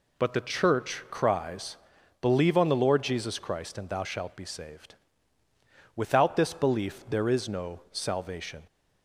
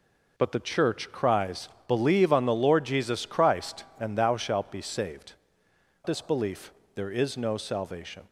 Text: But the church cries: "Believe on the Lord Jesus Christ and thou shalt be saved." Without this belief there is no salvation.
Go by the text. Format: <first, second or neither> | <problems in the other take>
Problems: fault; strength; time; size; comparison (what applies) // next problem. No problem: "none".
first | skips "Without"; at 5.6 s // pauses between "belief" and "there"; slight; at 6.7 s; 0.24 s long